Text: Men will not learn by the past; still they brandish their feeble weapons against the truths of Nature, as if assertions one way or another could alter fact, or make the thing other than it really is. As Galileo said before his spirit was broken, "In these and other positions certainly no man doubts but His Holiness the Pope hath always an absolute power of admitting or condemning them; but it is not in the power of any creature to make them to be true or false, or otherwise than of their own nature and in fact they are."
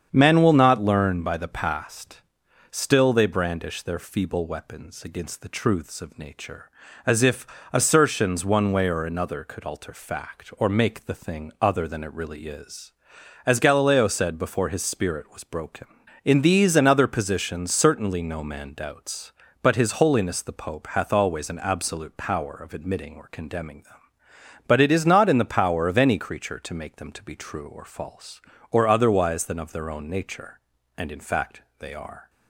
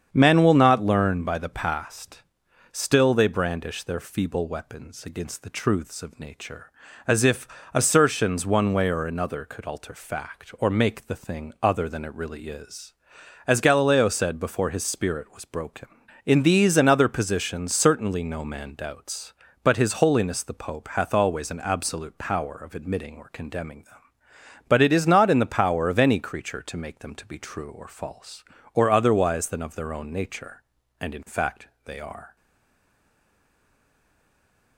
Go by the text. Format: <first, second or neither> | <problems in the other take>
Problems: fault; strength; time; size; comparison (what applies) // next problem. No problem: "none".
first | starts louder than the rest; strong; until 1.1 s; 7.5 dB; strong in the first // pauses between "if" and "assertions"; slight; at 7.4 s; 0.26 s long; slight in the first // pauses between "fact" and "they"; slight; at 31.6 s; 0.18 s long; slight in the first // stays silent after the last word; from 32.3 s on; 2.4 s long